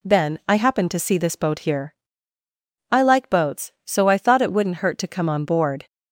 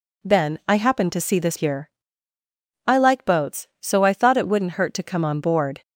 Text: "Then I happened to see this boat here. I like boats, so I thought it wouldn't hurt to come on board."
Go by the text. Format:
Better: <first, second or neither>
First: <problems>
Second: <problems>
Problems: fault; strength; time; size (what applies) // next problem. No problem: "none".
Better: first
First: none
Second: skips "boat"; at 1.5 s